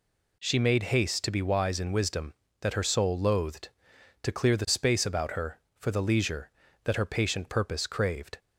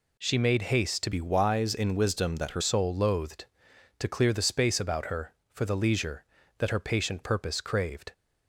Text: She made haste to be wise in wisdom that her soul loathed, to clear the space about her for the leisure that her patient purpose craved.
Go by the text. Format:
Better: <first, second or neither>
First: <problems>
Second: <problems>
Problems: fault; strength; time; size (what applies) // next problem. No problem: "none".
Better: first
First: none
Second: changes voice from "be" to "her"; from 1.1 to 2.6 s; 1.5 s long